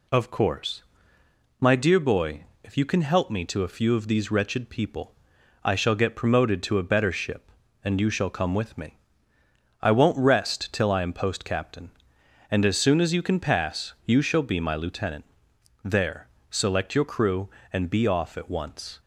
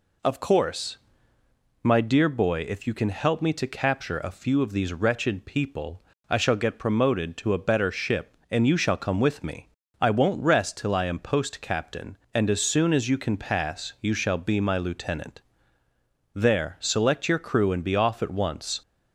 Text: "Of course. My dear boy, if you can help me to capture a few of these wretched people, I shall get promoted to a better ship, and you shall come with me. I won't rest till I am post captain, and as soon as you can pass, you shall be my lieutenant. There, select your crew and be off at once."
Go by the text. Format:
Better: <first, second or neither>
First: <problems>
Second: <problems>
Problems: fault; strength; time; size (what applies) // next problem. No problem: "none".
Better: second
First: skips "capture"; at 3.6 s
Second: none